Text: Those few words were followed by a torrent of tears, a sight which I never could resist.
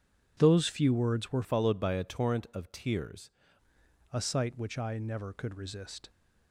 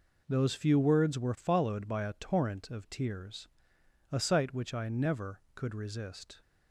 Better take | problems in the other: second | changes voice from "followed" to "tears"; from 1.4 to 3.3 s; 1.9 s long

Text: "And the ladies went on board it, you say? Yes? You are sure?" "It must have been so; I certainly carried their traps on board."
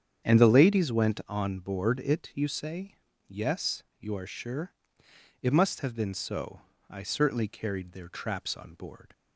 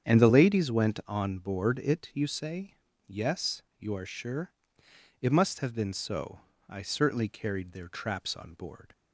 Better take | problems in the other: neither | starts louder than the rest; strong; the same in both

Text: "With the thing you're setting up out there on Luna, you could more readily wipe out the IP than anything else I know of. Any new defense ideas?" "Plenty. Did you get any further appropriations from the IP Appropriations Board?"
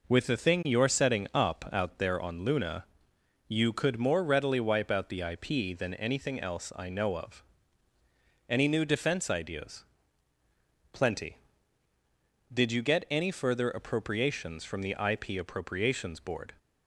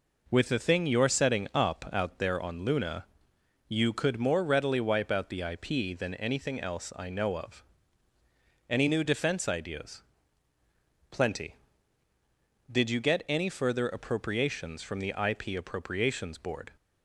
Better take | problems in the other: neither | none

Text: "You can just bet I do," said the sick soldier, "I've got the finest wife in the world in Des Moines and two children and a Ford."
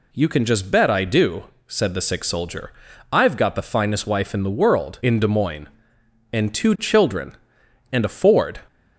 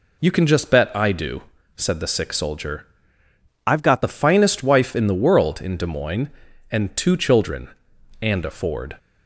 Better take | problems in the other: first | changes voice from "I've" to "got"; from 3.6 to 4.0 s; 0.4 s long

